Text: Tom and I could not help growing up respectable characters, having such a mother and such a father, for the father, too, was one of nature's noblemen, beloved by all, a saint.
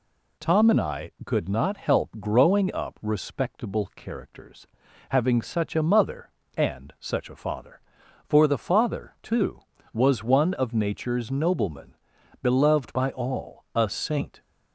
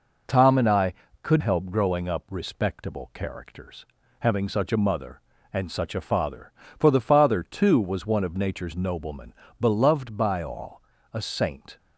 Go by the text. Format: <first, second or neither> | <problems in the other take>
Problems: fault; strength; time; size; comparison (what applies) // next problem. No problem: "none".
first | skips "not"; at 1.4 s